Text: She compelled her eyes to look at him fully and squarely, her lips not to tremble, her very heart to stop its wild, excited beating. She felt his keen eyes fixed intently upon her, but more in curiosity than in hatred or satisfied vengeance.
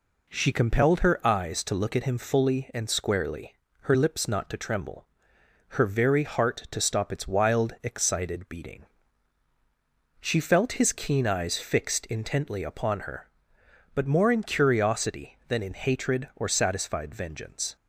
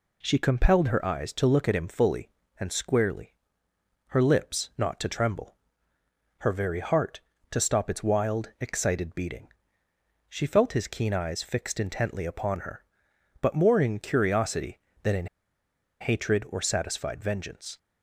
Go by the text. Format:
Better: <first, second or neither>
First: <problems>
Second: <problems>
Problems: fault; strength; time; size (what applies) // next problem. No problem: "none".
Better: first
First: none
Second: pauses between "in" and "hatred"; noticeable; at 15.2 s; 0.75 s long